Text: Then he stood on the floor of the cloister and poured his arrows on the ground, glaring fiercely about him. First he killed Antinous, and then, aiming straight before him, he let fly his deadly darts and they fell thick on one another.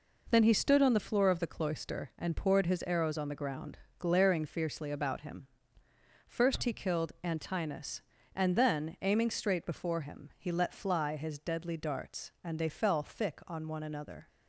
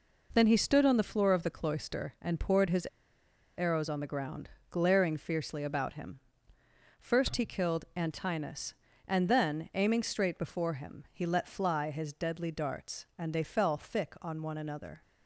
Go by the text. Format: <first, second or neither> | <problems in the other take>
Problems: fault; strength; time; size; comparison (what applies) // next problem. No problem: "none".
first | pauses between "his" and "arrows"; noticeable; at 2.8 s; 0.70 s long